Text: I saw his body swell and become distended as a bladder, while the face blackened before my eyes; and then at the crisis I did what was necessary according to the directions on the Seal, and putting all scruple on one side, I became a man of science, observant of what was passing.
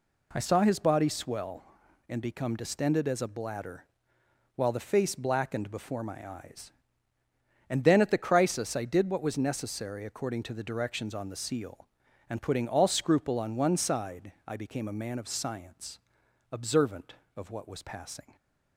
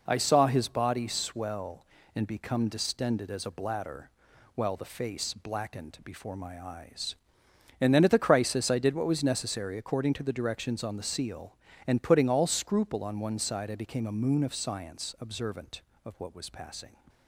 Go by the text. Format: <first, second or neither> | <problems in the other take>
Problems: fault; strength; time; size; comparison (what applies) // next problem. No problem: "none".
first | says "moon" for "man"; at 14.1 s